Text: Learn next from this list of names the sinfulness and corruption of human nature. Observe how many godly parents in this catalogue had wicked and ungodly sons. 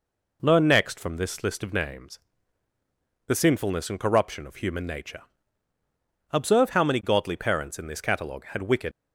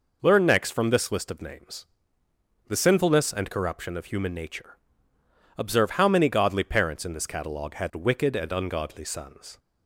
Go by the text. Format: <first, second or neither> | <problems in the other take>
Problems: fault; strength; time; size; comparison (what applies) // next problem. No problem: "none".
second | pauses between "names" and "the"; at 2.1 s; 1.0 s long; noticeable in the second // stops before "and ungodly sons"; at 8.9 s